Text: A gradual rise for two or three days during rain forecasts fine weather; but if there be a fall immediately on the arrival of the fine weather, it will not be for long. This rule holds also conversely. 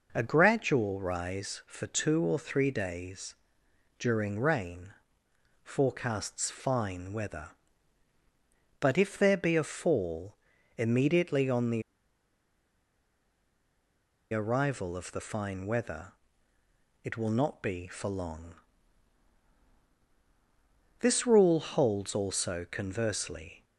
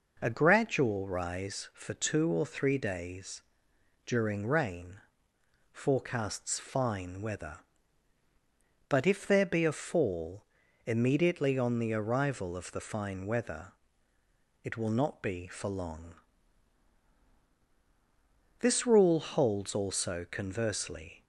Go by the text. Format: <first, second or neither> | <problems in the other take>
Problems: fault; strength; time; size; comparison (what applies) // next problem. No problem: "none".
second | pauses between "days" and "during"; noticeable; at 3.3 s; 0.64 s long; noticeable in the second // pauses between "rain" and "forecasts"; noticeable; at 4.8 s; 0.74 s long; noticeable in the second // pauses between "fall" and "immediately"; at 10.3 s; 0.42 s long; also in the second // pauses between "the" and "arrival"; strong; at 11.8 s; 2.5 s long